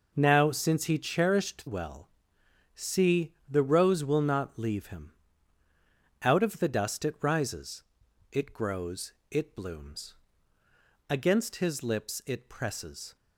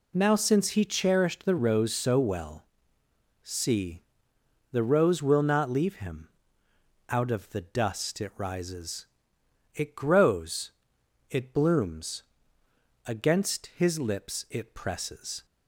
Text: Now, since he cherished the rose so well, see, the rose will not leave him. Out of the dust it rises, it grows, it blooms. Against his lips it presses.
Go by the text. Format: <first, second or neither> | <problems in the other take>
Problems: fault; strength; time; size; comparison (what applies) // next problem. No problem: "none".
second | skips "the rose so"; at 1.6 s